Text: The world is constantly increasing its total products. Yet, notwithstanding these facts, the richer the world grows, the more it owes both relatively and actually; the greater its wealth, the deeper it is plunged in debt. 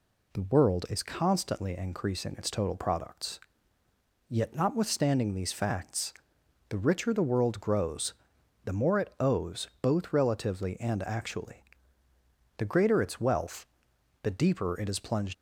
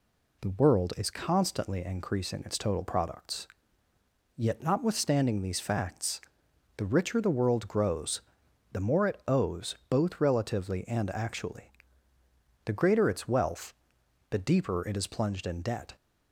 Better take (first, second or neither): second